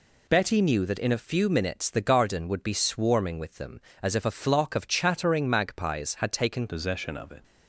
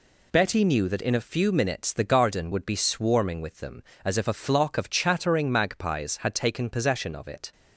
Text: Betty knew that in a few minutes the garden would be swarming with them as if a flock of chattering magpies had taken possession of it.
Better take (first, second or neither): second